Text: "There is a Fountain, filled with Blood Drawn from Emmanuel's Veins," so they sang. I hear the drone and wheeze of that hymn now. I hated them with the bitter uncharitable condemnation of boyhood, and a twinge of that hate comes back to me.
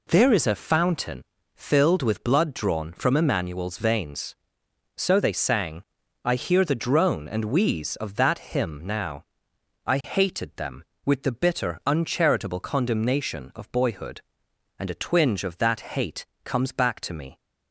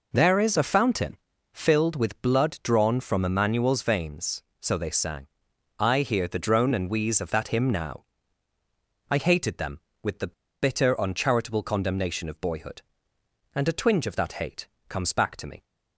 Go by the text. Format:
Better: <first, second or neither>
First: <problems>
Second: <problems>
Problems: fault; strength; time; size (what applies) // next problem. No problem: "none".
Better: first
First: pauses between "hate" and "comes"; slight; at 16.2 s; 0.18 s long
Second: pauses between "the" and "bitter"; slight; at 10.3 s; 0.28 s long // pauses between "hate" and "comes"; slight; at 14.6 s; 0.22 s long